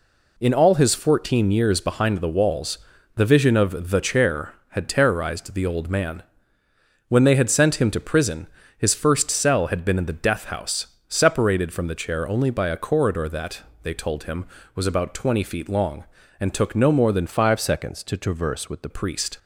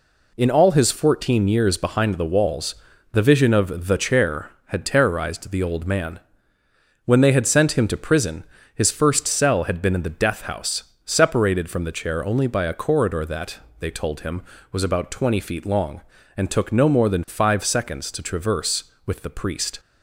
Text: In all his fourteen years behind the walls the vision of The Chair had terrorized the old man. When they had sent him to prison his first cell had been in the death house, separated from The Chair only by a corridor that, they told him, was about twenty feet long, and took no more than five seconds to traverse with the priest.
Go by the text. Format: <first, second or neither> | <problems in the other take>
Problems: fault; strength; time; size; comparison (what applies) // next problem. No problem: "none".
second | pauses between "walls" and "the"; at 2.7 s; 0.38 s long; also in the second // pauses between "prison" and "his"; slight; at 8.4 s; 0.30 s long; slight in the second // changes voice from "five" to "the"; from 17.2 to 18.8 s; 1.6 s long